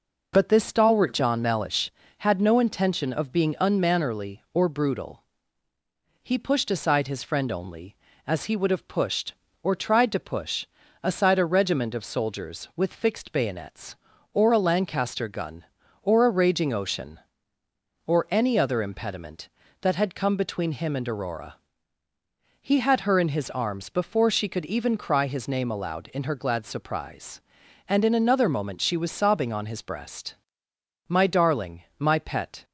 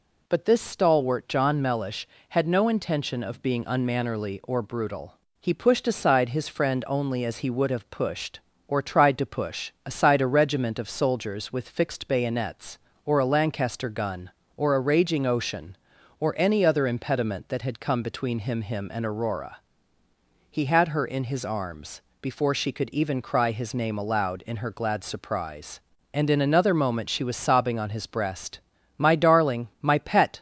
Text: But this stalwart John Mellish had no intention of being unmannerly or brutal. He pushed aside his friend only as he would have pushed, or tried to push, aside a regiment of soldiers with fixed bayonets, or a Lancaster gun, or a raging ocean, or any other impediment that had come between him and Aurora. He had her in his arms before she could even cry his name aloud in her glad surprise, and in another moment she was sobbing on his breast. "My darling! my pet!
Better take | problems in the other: first | says "him" twice; at 18.6 s // pauses between "arms" and "before"; slight; at 22.0 s; 0.18 s long

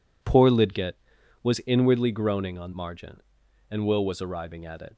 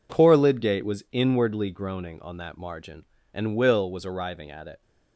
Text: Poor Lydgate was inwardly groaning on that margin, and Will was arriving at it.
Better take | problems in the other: second | skips "that"; at 2.7 s

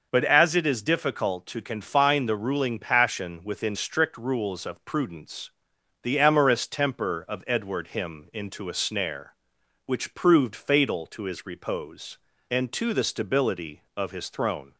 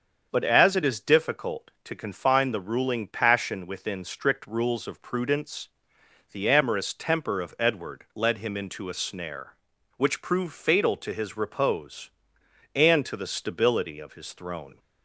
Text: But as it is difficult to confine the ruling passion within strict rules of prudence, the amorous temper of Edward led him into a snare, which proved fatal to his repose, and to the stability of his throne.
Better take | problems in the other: second | starts louder than the rest; noticeable; until 1.1 s; 6 dB; also in the second // skips "led"; at 7.8 s

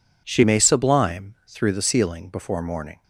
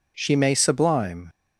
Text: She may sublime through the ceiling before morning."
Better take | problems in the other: first | stops before "through the ceiling before morning"; at 1.2 s

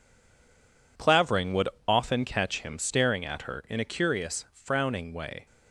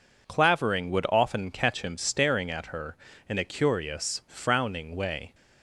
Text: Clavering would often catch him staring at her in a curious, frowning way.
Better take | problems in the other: second | stays silent before the first word; until 0.9 s; 0.9 s long // pauses between "would" and "often"; slight; at 1.6 s; 0.20 s long

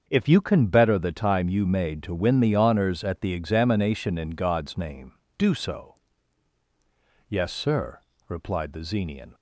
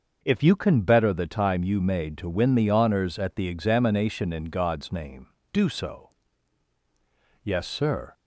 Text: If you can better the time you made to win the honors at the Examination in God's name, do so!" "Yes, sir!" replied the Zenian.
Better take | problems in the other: first | starts louder than the rest; until 1.2 s; 6 dB; also in the first // stops before "replied the Zenian"; at 8.1 s

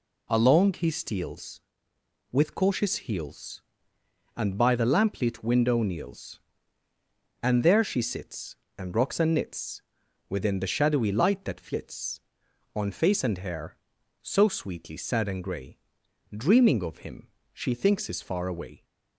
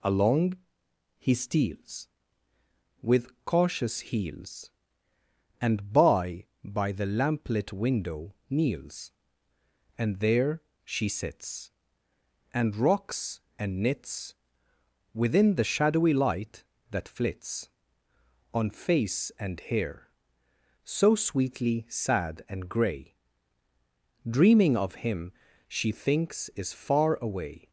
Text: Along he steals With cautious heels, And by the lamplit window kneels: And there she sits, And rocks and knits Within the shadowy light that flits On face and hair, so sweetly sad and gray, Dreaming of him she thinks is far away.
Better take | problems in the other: first | pauses between "Along" and "he"; noticeable; at 0.5 s; 0.62 s long // pauses between "With" and "cautious"; slight; at 3.2 s; 0.16 s long // says "by" twice; at 6.6 s // pauses between "window" and "kneels"; slight; at 8.3 s; 0.16 s long // pauses between "there" and "she"; slight; at 10.6 s; 0.22 s long // pauses between "knits" and "Within"; noticeable; at 14.3 s; 0.80 s long; noticeable in the first // pauses between "him" and "she"; slight; at 25.3 s; 0.36 s long; slight in the first

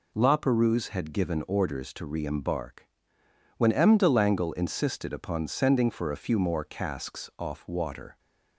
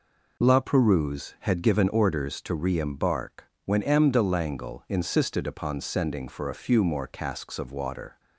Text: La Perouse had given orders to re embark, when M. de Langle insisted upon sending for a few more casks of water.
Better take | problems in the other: second | says "off" for "of"; at 7.3 s

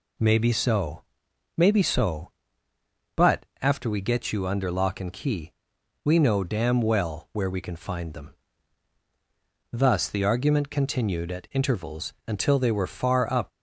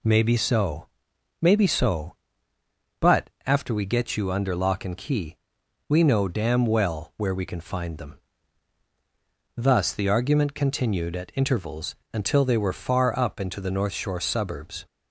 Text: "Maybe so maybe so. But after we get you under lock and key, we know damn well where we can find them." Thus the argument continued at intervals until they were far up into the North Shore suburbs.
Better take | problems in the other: second | pauses between "so" and "maybe"; noticeable; at 1.0 s; 0.54 s long; noticeable in the second // pauses between "But" and "after"; slight; at 3.4 s; 0.16 s long; slight in the second // pauses between "intervals" and "until"; slight; at 12.1 s; 0.16 s long; slight in the second // stops before "into the North Shore suburbs"; at 13.5 s

